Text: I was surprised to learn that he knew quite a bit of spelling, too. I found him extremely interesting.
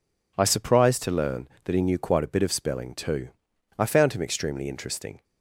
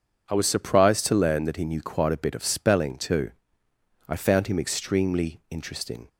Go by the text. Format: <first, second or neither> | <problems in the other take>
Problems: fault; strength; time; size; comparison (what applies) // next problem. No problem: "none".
second | skips "was"; at 0.4 s